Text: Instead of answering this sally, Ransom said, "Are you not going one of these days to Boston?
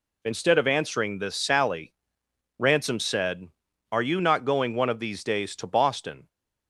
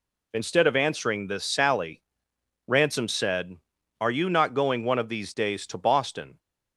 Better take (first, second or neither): neither